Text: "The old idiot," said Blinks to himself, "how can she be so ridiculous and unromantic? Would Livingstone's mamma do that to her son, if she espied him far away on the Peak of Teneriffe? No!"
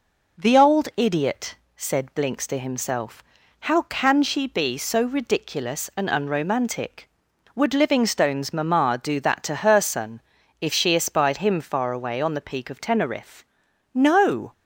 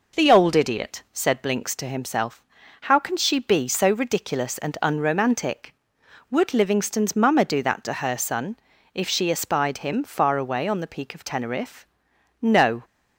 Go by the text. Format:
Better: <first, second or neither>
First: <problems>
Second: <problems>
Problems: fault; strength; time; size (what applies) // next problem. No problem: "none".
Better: neither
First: none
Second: none